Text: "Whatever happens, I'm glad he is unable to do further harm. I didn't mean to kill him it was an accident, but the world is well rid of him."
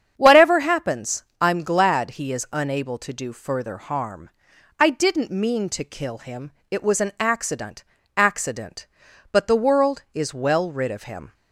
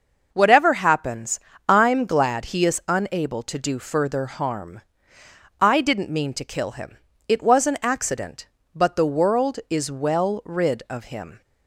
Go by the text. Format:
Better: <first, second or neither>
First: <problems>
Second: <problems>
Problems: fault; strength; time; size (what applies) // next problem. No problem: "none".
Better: second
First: starts louder than the rest; strong; until 1.1 s; 8 dB // pauses between "him" and "it"; slight; at 6.5 s; 0.20 s long // says "accident" twice; at 8.1 s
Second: pauses between "him" and "it"; slight; at 6.9 s; 0.30 s long